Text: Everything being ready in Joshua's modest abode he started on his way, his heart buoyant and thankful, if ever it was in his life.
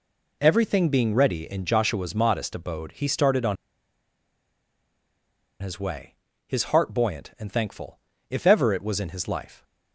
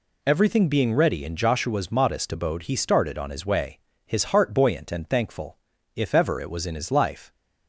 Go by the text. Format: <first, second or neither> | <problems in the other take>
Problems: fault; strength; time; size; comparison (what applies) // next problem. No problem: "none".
second | pauses between "on" and "his"; strong; at 3.5 s; 2.0 s long